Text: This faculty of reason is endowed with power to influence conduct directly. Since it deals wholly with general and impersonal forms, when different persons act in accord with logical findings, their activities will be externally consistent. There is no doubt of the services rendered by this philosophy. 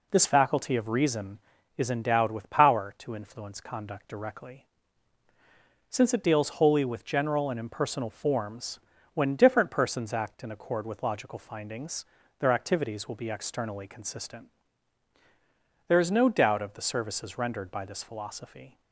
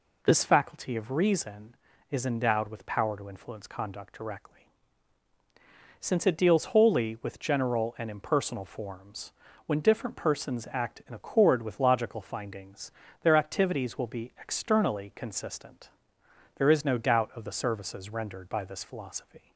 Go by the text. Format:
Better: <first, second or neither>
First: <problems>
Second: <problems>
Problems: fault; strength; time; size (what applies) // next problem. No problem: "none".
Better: neither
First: none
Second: none